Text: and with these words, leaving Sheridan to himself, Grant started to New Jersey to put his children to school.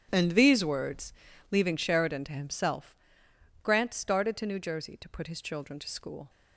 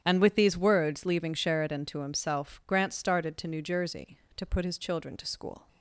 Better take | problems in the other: second | starts louder than the rest; strong; until 1.1 s; 10.5 dB; strong in the second // skips "with"; at 0.3 s

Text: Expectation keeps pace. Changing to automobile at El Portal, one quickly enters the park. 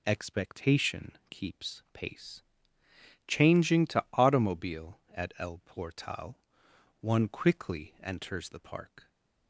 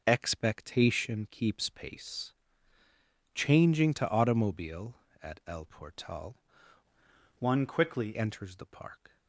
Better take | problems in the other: first | changes voice from "one" to "quickly"; from 7.3 to 8.1 s; 0.8 s long

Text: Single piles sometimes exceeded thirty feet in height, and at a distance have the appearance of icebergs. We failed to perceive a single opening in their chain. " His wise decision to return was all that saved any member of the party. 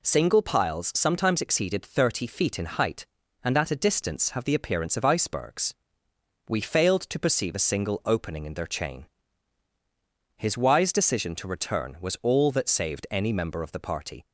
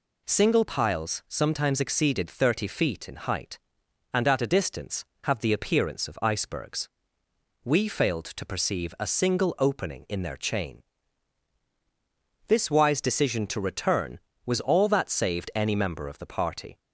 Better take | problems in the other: first | says "This" for "His"; at 12.4 s

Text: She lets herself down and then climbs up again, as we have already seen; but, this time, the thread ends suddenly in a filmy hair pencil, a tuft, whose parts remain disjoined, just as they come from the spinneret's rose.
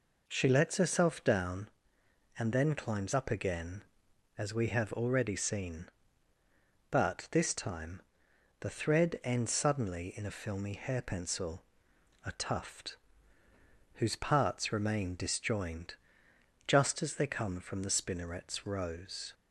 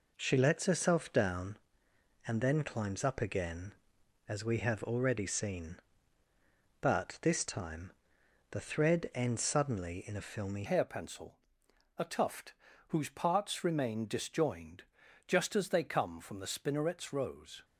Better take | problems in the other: first | changes voice at "hair"; from 10.6 s on; 7.0 s long

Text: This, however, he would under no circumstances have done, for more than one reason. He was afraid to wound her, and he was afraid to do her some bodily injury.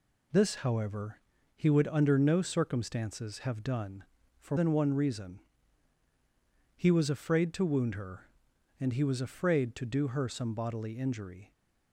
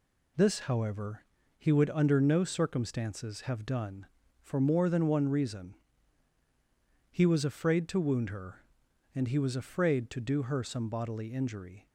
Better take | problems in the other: second | skips "more"; at 4.5 s

